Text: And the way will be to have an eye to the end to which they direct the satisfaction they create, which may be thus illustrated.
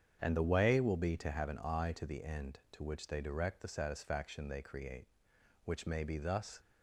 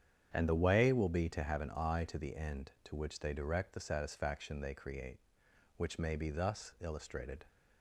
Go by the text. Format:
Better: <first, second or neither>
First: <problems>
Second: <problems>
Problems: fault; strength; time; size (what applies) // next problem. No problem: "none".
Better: second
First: starts louder than the rest; strong; until 1.2 s; 8 dB // stops before "illustrated"; at 6.6 s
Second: starts louder than the rest; strong; until 1.3 s; 9 dB